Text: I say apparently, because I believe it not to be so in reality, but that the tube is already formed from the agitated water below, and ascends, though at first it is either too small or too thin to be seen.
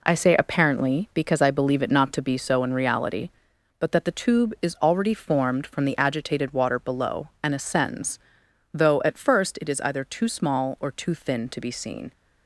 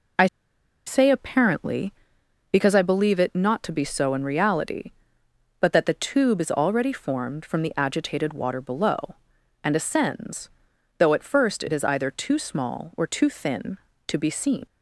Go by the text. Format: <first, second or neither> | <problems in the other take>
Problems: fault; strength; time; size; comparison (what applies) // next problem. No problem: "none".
first | pauses between "I" and "say"; noticeable; at 0.2 s; 0.60 s long